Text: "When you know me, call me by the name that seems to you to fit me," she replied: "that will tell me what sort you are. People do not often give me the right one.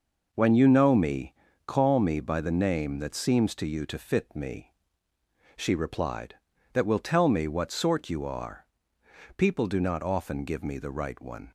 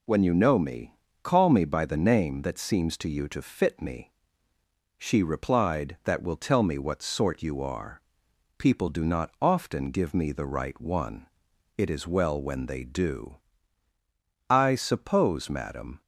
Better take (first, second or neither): first